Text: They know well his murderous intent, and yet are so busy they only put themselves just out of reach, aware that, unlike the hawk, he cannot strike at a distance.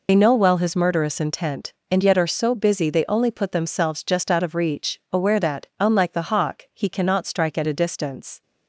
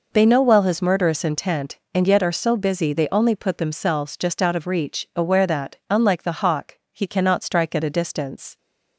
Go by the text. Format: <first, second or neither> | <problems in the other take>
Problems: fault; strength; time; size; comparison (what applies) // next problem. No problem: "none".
second | loses the start of "They"; at 0.0 s; 55 ms